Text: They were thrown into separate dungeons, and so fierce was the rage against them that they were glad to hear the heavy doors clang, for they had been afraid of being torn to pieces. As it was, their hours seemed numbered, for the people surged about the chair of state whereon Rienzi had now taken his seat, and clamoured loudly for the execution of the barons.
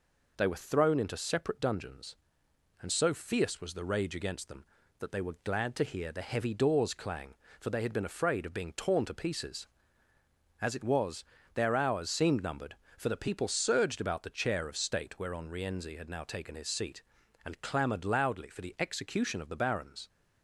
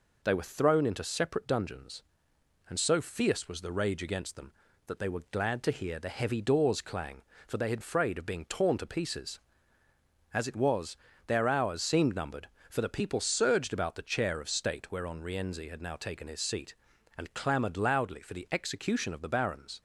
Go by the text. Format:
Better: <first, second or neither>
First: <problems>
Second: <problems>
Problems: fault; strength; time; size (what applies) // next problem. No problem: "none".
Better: first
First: none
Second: skips "been"; at 7.7 s